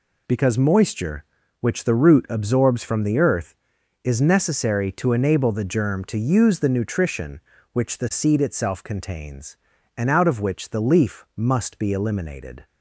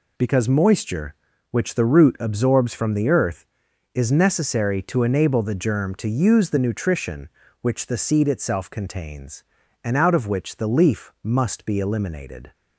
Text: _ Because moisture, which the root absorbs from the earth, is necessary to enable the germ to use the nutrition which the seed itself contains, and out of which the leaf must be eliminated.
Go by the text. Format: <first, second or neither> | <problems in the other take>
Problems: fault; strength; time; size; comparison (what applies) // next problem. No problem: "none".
neither | none